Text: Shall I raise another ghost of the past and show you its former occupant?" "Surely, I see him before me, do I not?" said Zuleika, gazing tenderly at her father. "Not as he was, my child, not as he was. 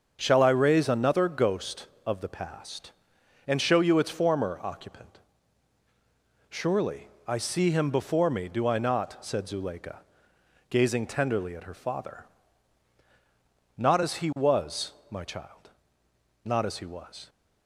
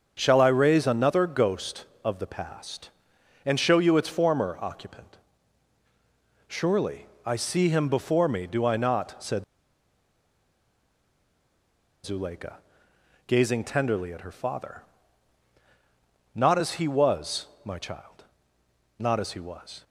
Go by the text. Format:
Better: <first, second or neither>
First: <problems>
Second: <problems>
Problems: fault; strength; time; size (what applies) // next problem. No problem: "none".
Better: first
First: starts louder than the rest; until 1.2 s; 7 dB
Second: starts louder than the rest; until 1.1 s; 7 dB // pauses between "said" and "Zuleika"; strong; at 9.4 s; 2.6 s long